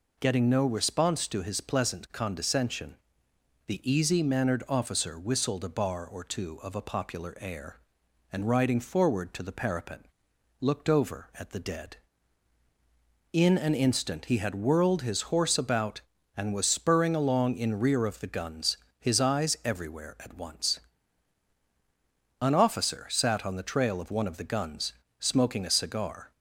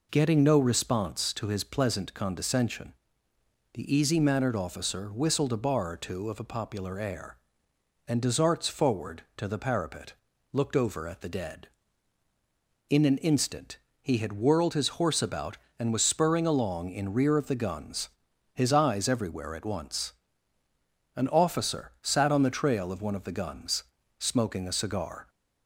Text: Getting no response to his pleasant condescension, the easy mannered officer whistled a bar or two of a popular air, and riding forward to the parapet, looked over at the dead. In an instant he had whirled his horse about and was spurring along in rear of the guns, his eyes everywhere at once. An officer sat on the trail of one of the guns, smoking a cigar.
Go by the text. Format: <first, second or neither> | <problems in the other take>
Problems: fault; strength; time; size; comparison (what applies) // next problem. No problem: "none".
first | says "desarts" for "riding"; at 8.2 s // pauses between "instant" and "he"; slight; at 13.7 s; 0.24 s long